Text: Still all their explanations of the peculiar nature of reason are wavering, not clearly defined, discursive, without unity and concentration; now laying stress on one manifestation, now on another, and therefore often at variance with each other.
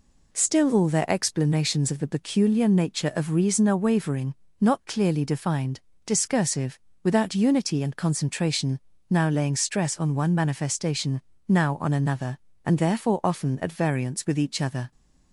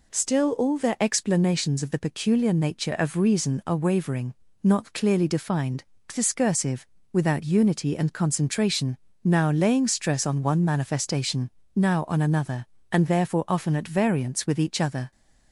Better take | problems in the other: neither | none

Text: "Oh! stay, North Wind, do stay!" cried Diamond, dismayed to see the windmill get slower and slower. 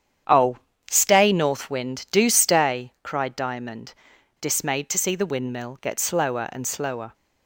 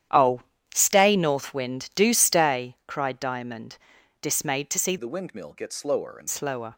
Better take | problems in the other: first | starts louder than the rest; strong; until 1.4 s; 10.5 dB; strong in the first // changes voice from "the" to "and"; from 4.9 to 6.2 s; 1.3 s long

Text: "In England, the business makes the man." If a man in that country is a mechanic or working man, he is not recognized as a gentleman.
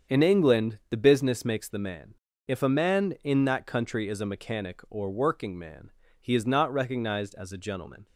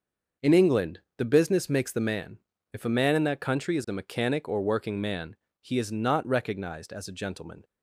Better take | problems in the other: neither | starts louder than the rest; the same in both

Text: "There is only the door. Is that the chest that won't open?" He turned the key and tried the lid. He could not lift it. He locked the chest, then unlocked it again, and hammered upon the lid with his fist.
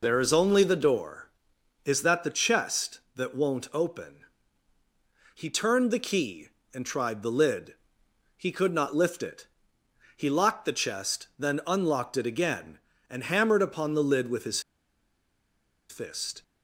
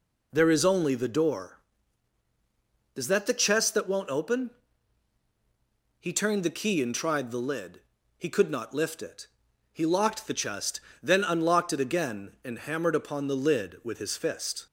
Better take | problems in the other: second | pauses between "his" and "fist"; strong; at 14.5 s; 1.2 s long

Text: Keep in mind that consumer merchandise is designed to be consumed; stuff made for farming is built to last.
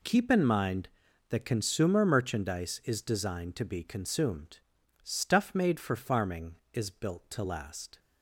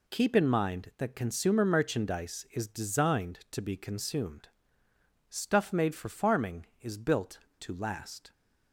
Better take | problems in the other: neither | none

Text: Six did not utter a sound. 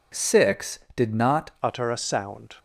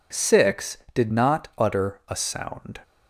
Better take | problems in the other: second | changes voice at "utter"; from 1.6 s on; 0.9 s long

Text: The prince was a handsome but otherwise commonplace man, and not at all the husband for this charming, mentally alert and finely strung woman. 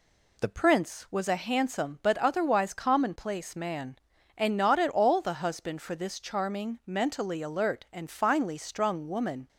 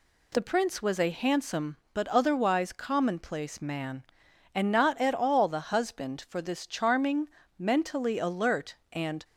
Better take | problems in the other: first | stops before "finely strung woman"; at 9.2 s

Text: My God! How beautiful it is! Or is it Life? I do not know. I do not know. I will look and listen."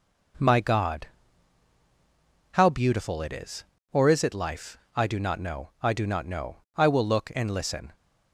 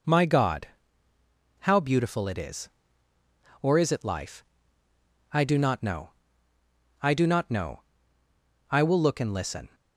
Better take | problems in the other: neither | none

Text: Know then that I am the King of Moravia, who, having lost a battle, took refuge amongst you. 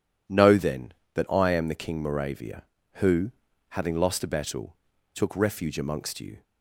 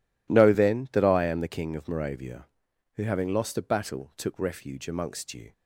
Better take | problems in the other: second | skips "of"; at 2.0 s

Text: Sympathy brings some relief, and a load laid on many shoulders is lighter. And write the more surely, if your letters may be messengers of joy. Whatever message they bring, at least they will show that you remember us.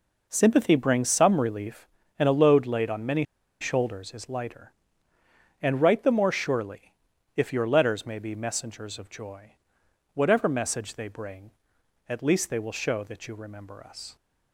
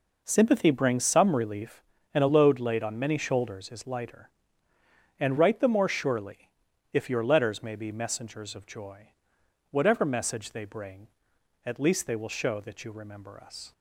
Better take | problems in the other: second | pauses between "many" and "shoulders"; at 3.2 s; 0.36 s long

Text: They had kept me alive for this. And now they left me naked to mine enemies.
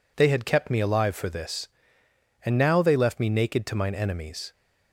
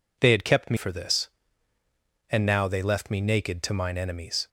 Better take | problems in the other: first | skips "alive"; at 0.7 s

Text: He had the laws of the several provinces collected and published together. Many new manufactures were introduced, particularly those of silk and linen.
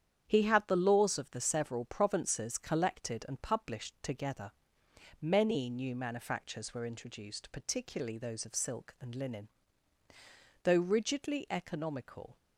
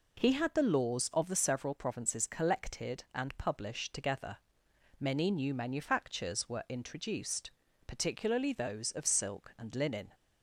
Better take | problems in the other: second | starts louder than the rest; strong; until 1.2 s; 9 dB // goes on to say "Though rigidly economical"; strong; from 10.6 s on; 1.7 s long

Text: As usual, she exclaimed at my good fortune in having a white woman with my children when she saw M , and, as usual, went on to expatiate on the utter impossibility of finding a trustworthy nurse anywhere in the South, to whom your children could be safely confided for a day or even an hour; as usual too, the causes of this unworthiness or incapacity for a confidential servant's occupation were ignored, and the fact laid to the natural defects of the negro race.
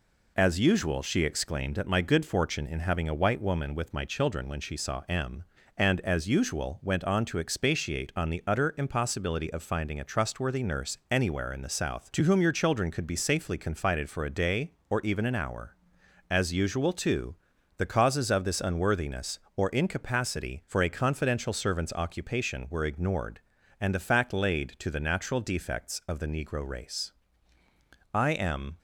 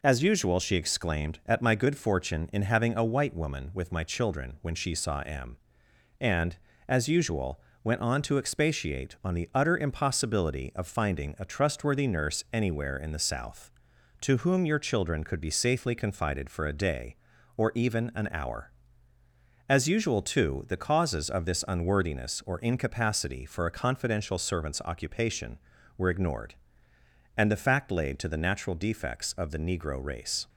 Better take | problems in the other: second | goes on to say "I am"; noticeable; from 28.1 s on; 0.64 s long

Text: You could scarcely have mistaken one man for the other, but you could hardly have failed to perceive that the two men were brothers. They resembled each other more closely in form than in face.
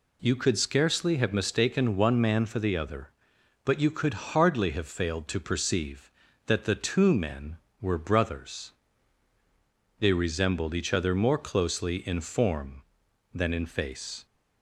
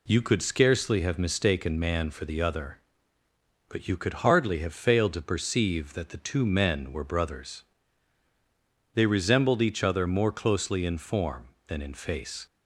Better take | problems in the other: first | skips "one"; at 1.8 s

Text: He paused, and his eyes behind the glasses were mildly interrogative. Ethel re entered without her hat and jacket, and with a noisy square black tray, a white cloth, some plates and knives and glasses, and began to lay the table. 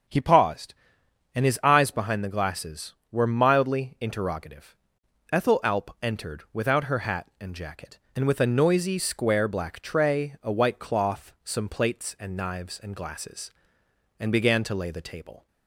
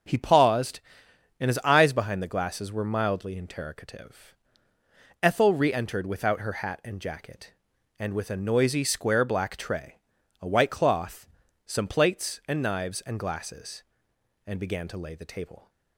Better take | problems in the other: second | starts louder than the rest; strong; until 1.7 s; 7 dB; also in the second // says "alp" for "re"; at 5.6 s

